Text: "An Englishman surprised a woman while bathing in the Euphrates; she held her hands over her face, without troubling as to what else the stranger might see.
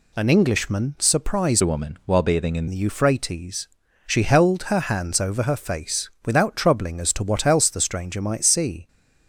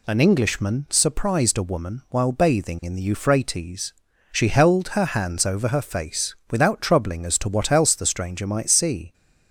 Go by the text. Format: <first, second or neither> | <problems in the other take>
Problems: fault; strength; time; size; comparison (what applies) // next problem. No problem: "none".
second | changes voice from "a" to "in"; from 1.6 to 2.6 s; 1.0 s long